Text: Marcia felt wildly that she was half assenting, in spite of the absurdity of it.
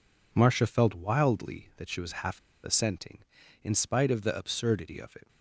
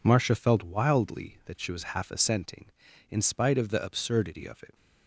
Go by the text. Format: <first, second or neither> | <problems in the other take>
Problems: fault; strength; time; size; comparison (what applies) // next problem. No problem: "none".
second | pauses between "half" and "assenting"; slight; at 2.3 s; 0.24 s long